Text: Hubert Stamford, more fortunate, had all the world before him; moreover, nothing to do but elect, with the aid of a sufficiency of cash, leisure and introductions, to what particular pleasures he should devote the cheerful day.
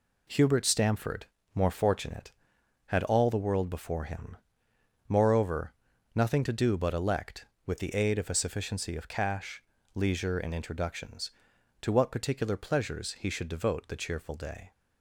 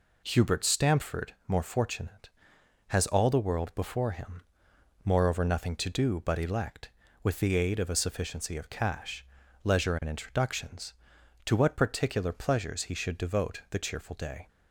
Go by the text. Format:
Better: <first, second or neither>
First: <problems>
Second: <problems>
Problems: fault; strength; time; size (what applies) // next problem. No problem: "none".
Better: first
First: none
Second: says "has" for "had"; at 2.8 s